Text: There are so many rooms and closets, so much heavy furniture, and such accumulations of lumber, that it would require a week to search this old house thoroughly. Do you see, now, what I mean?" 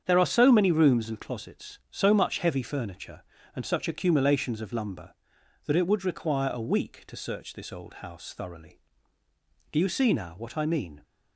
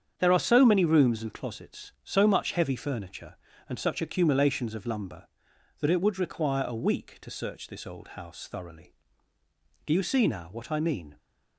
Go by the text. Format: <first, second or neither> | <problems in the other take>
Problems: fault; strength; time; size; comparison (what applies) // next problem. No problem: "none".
neither | starts louder than the rest; strong; the same in both